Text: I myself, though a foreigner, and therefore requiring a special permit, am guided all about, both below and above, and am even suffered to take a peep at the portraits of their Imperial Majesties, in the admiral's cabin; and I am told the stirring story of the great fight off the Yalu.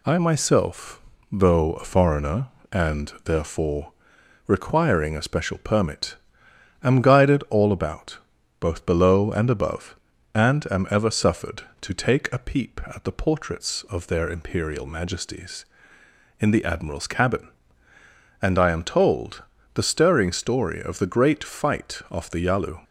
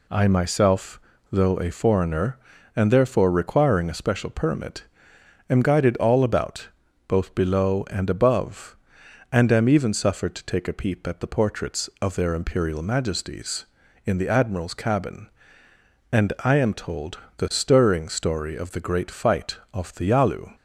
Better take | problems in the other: second | pauses between "therefore" and "requiring"; noticeable; at 3.9 s; 0.54 s long // says "ever" for "even"; at 10.8 s // pauses between "told" and "the"; slight; at 19.4 s; 0.30 s long; slight in the second

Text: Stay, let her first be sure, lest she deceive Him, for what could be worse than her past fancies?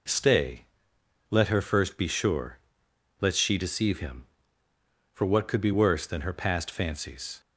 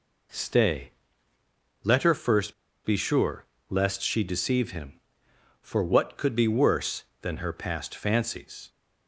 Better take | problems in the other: first | pauses between "first" and "be"; slight; at 2.5 s; 0.31 s long

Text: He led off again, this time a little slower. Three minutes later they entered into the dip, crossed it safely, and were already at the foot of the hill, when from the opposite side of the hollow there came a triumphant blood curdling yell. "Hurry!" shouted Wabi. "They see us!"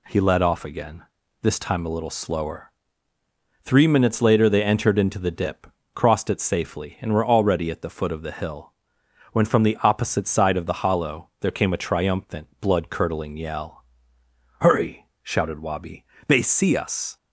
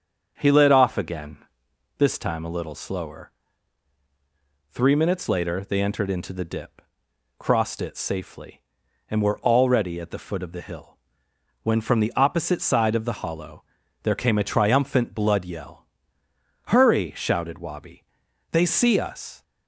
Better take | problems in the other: first | starts louder than the rest; until 1.3 s; 7 dB // pauses between "hollow" and "there"; at 13.6 s; 0.40 s long // skips "curdling"; at 15.4 s

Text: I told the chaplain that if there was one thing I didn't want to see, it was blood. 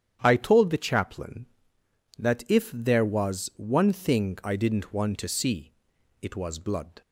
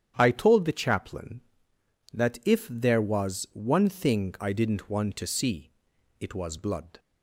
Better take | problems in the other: neither | starts louder than the rest; strong; the same in both

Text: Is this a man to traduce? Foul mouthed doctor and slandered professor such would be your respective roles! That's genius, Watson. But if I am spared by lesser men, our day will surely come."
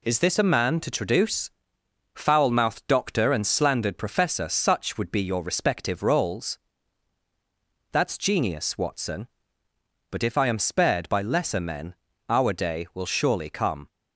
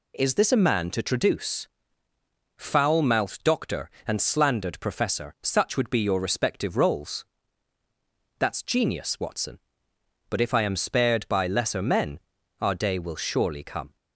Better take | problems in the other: neither | none

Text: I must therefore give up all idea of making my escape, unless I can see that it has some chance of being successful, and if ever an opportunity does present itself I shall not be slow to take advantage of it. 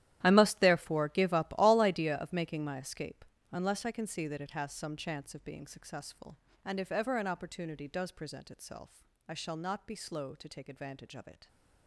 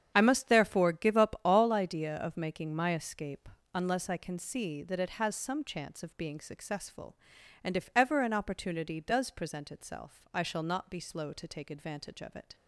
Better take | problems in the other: second | gets quieter; strong; throughout; 16 dB // starts louder than the rest; strong; until 1.2 s; 12.5 dB; strong in the second // pauses between "itself" and "I"; slight; at 9.0 s; 0.24 s long

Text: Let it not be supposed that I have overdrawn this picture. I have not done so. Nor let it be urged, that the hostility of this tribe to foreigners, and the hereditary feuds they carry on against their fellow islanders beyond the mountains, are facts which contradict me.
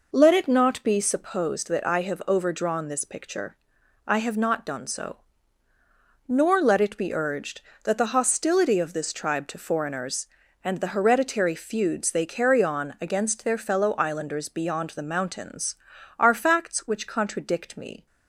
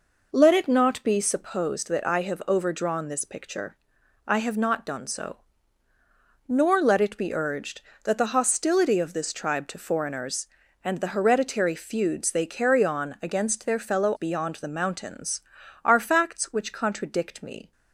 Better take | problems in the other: first | skips "islanders"; at 14.1 s

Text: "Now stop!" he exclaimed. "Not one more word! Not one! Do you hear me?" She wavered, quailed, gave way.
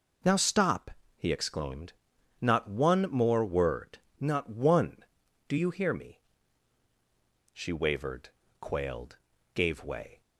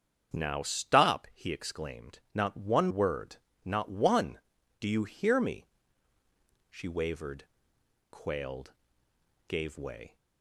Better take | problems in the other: first | starts louder than the rest; strong; until 1.4 s; 7.5 dB // skips "more"; at 2.8 s

